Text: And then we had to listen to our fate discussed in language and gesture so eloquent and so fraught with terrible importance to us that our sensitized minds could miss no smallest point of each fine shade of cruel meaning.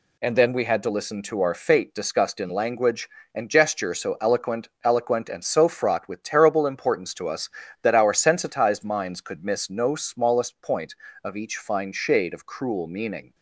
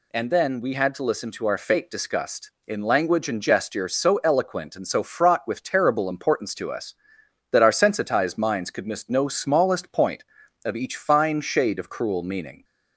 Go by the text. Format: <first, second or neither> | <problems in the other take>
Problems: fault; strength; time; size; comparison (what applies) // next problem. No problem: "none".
second | says "eloquent" twice; at 4.8 s